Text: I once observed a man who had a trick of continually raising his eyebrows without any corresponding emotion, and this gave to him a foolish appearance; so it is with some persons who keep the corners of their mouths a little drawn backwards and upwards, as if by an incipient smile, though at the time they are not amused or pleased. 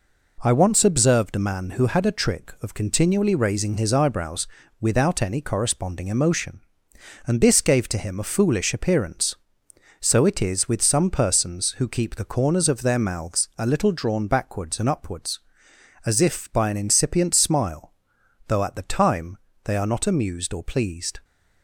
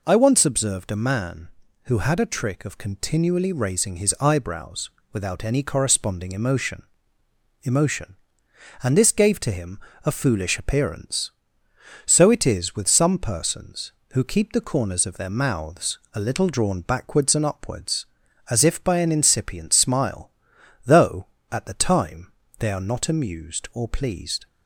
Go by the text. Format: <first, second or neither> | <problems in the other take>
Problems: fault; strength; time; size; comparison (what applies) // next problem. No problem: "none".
first | pauses between "eyebrows" and "without"; slight; at 4.8 s; 0.24 s long; slight in the first // says "emotion" twice; at 7.6 s // pauses between "him" and "a"; slight; at 9.7 s; 0.26 s long // pauses between "time" and "they"; slight; at 22.2 s; 0.30 s long; slight in the first